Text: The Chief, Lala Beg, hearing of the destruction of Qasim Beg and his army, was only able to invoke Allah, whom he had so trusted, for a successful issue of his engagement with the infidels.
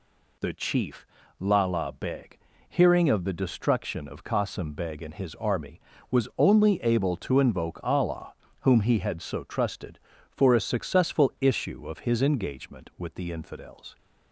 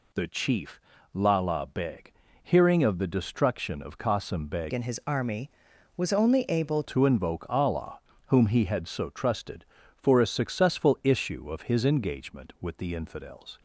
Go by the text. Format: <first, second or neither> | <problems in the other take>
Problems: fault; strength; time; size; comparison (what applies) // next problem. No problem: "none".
first | changes voice from "and" to "able"; from 4.7 to 6.8 s; 2.1 s long